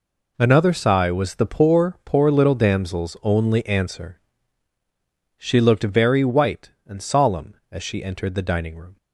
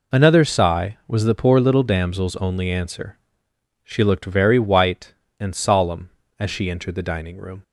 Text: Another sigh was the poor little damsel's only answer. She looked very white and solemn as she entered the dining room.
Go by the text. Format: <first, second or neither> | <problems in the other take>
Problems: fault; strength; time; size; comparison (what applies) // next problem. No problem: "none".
second | says "poor" twice; at 2.0 s